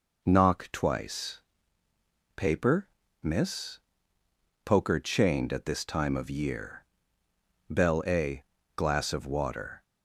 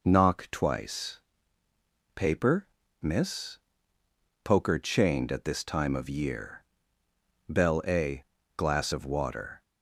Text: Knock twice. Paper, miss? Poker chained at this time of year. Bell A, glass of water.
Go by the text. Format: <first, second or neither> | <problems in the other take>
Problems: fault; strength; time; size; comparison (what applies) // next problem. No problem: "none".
neither | none